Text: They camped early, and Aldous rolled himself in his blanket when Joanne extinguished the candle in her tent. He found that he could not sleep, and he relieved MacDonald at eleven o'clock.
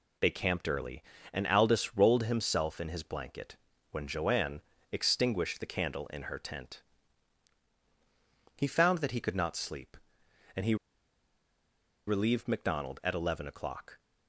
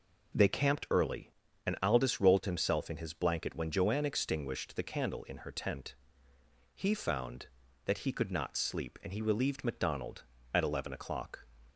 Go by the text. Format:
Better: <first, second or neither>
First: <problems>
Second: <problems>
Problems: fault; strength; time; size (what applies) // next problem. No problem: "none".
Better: second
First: pauses between "blanket" and "when"; slight; at 3.5 s; 0.36 s long // pauses between "Joanne" and "extinguished"; slight; at 4.6 s; 0.30 s long // pauses between "he" and "relieved"; strong; at 10.7 s; 1.3 s long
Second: none